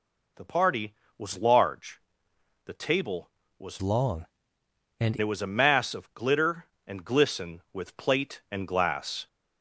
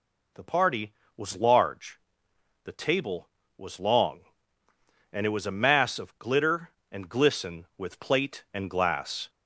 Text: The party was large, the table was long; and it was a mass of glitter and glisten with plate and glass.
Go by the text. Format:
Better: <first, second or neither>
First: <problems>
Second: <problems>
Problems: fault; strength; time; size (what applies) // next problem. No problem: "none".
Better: second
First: changes voice from "long" to "and"; from 3.8 to 5.1 s; 1.3 s long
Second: none